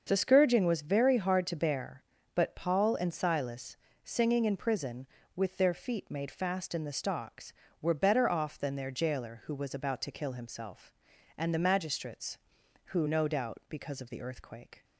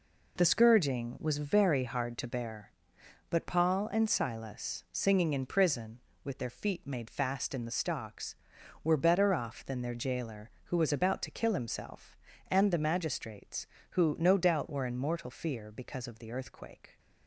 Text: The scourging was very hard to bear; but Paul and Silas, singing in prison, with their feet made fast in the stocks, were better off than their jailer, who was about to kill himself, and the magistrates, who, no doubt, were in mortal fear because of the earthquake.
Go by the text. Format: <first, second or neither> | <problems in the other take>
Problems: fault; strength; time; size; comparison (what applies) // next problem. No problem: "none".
second | starts louder than the rest; until 1.0 s; 6.5 dB // skips "were in mortal fear"; at 13.6 s